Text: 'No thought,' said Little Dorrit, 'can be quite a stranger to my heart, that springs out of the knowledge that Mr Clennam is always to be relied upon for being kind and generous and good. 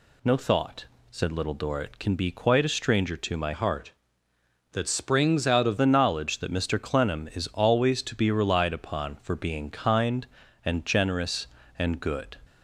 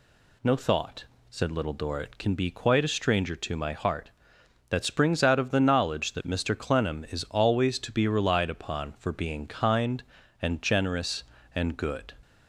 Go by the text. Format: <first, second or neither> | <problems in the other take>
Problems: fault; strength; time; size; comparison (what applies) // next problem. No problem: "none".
second | changes voice from "heart" to "of"; from 3.5 to 5.7 s; 2.2 s long